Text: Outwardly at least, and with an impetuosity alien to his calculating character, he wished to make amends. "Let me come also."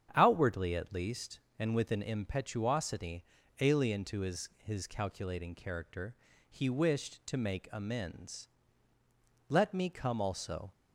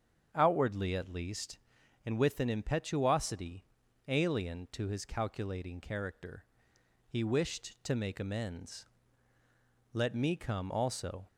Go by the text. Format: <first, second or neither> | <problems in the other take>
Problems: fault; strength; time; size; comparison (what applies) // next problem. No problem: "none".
second | starts louder than the rest; strong; until 1.1 s; 8.5 dB; strong in the second // pauses between "impetuosity" and "alien"; slight; at 3.2 s; 0.36 s long; also in the second // says "his" twice; at 4.5 s